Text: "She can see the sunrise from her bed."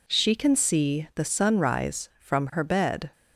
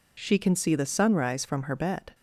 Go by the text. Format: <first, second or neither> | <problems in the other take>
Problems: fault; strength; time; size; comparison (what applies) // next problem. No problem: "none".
neither | none